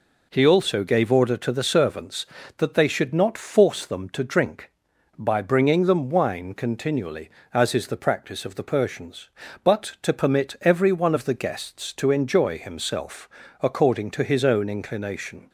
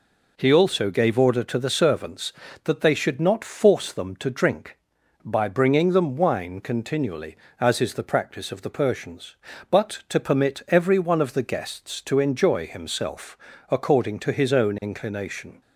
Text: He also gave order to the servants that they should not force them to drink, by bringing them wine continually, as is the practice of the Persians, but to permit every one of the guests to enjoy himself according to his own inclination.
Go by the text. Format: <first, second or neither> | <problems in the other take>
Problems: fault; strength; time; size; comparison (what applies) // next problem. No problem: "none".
neither | pauses between "himself" and "according"; slight; the same in both